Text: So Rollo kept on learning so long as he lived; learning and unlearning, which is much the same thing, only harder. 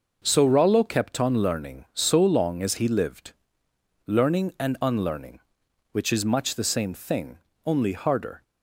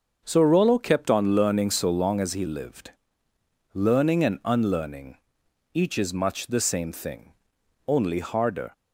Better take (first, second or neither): first